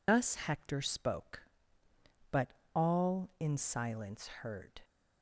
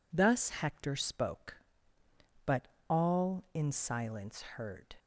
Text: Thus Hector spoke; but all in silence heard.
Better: second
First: loses the start of "Thus"; at 0.0 s; 105 ms // pauses between "but" and "all"; slight; at 2.5 s; 0.22 s long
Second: pauses between "but" and "all"; slight; at 2.6 s; 0.22 s long

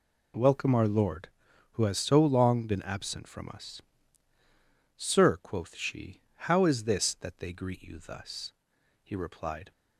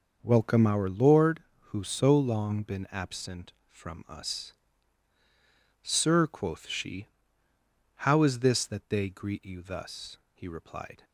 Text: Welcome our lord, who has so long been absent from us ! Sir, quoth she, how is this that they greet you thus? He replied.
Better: first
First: none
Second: starts louder than the rest; noticeable; until 1.2 s; 6 dB // skips "has"; at 1.8 s

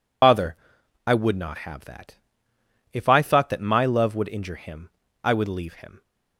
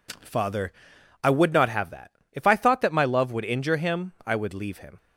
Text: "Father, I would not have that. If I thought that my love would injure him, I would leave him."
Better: second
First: loses the start of "Father"; at 0.2 s; 140 ms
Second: none

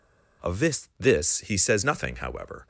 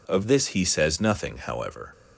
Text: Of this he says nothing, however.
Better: second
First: says "this" twice; at 0.9 s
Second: none

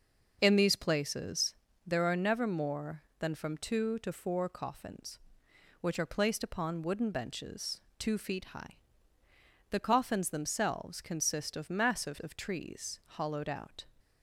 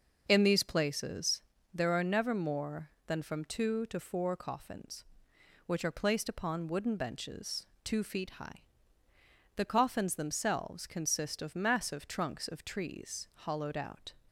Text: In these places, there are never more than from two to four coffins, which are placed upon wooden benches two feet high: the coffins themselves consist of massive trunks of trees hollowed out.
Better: second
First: pauses between "benches" and "two"; slight; at 7.8 s; 0.16 s long // skips "trunks"; at 12.1 s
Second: pauses between "benches" and "two"; slight; at 7.6 s; 0.16 s long

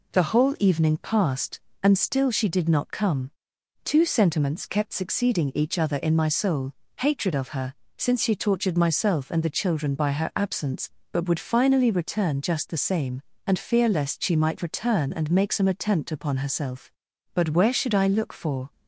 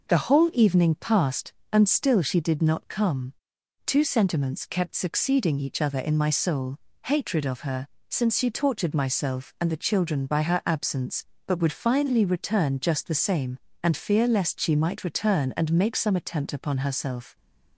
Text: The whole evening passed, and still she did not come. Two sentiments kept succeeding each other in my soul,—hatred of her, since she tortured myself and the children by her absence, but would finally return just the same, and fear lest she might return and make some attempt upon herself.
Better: second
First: goes on to say "But where should I look for"; from 17.3 s on; 1.3 s long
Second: none

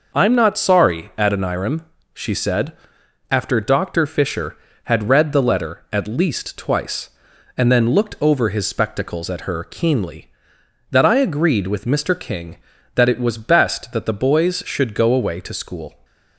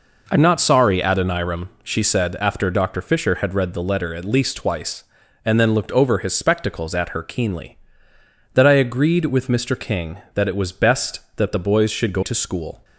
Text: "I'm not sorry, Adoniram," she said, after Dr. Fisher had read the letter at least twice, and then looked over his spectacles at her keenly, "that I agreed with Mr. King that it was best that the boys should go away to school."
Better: first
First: none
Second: skips "away"; at 12.2 s

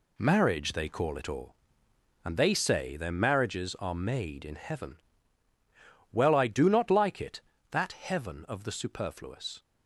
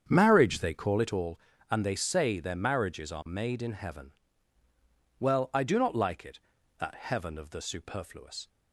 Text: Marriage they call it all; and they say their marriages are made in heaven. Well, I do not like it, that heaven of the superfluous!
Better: first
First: none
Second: starts louder than the rest; strong; until 1.4 s; 8 dB

